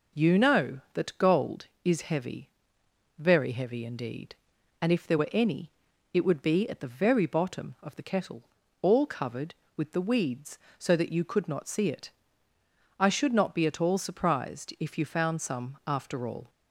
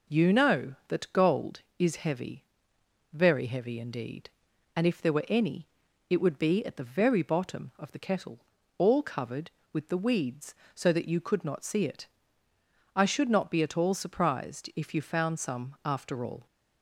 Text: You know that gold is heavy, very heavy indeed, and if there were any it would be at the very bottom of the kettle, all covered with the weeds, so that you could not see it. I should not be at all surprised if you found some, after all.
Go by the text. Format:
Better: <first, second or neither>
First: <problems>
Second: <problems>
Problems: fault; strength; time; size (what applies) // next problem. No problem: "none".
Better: neither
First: pauses between "any" and "it"; at 5.7 s; 0.42 s long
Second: pauses between "any" and "it"; at 5.6 s; 0.42 s long